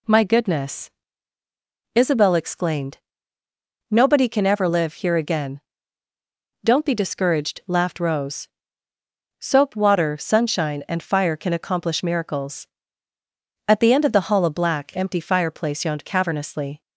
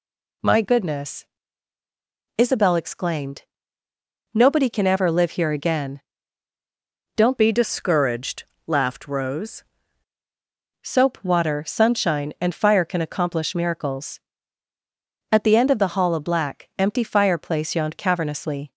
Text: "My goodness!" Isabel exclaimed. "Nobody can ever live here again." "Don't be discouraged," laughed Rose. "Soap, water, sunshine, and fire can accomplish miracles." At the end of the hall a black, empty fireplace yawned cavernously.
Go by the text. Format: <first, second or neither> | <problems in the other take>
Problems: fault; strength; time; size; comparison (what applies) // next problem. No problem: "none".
first | changes voice from "be" to "Rose"; from 7.3 to 9.6 s; 2.3 s long